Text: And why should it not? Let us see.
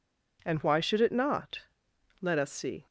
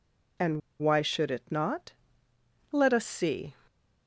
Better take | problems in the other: first | pauses between "And" and "why"; slight; at 0.6 s; 0.20 s long

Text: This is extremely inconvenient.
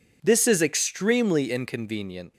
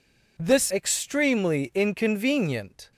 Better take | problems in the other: first | skips "is"; at 0.6 s

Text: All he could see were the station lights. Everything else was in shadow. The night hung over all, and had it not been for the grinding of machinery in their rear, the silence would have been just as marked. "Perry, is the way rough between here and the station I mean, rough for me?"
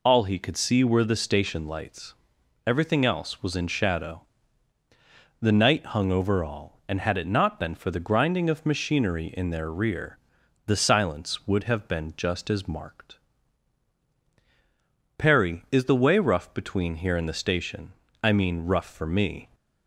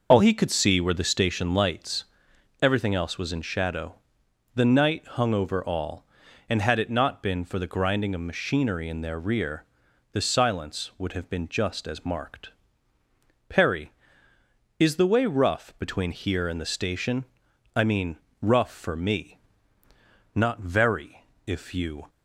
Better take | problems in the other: first | pauses between "station" and "I"; noticeable; at 17.2 s; 0.50 s long; slight in the first // goes on to say "Not very if you"; strong; from 20.3 s on; 1.7 s long

